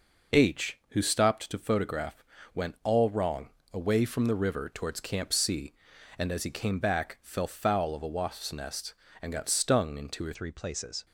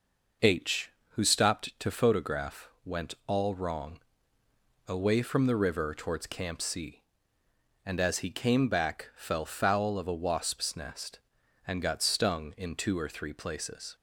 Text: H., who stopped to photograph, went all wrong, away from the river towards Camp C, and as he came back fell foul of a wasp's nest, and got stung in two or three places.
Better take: second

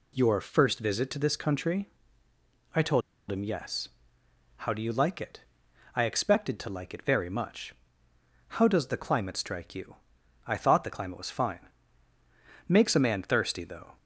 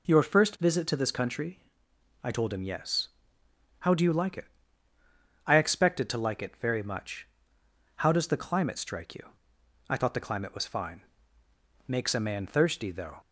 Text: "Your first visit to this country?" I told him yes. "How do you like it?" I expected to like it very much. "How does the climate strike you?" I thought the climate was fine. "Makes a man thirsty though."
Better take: second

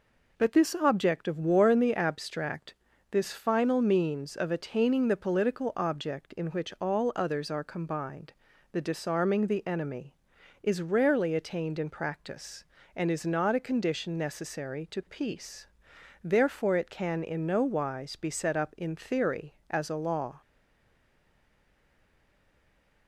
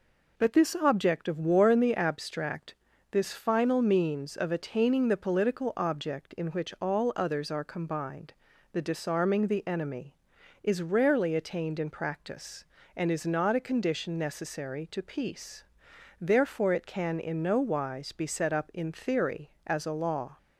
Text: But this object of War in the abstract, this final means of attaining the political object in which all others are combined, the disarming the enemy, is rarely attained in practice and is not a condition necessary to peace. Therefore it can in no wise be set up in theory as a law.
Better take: second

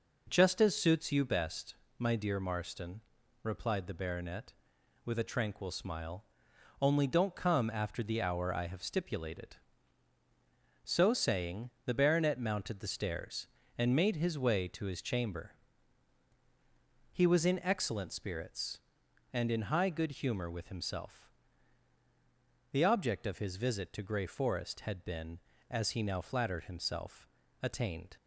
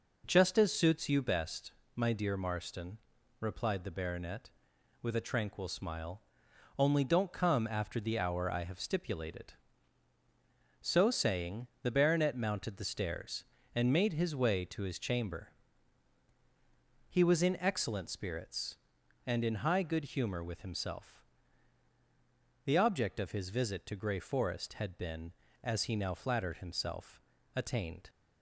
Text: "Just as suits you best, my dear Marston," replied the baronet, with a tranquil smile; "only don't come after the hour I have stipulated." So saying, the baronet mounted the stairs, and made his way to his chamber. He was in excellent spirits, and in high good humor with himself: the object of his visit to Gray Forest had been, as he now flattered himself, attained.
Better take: neither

